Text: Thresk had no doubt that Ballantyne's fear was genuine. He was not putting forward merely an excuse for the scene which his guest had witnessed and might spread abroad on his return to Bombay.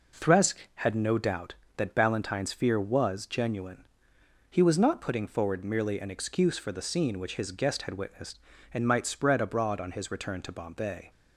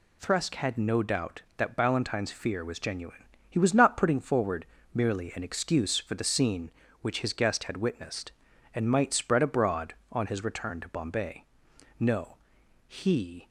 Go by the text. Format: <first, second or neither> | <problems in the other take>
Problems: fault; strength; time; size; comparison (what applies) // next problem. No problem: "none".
first | pauses between "forward" and "merely"; slight; at 4.6 s; 0.28 s long // goes on to say "No he"; from 11.9 s on; 1.5 s long